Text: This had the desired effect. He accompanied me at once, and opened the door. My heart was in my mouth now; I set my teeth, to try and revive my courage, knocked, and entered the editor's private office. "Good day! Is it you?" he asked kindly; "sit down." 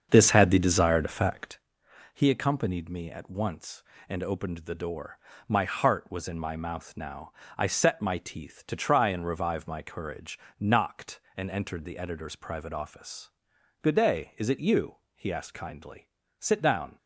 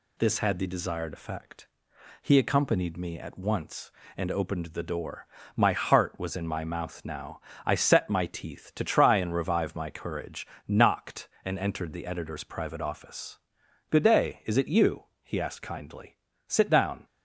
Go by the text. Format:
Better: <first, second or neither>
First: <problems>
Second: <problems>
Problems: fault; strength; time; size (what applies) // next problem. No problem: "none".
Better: second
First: starts louder than the rest; strong; until 1.6 s; 7 dB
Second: none